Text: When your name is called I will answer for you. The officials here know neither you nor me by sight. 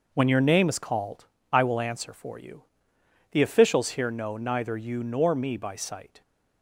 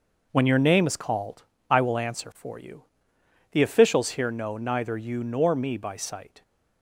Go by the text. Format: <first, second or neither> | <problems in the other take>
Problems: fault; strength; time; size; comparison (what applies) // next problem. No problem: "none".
neither | pauses between "called" and "I"; slight; the same in both